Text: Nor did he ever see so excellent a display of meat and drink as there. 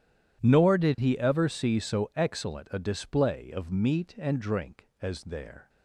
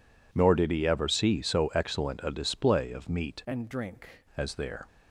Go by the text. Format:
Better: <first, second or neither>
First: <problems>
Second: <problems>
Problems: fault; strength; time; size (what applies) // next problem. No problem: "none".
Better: first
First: none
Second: changes voice from "and" to "drink"; from 3.4 to 4.0 s; 0.6 s long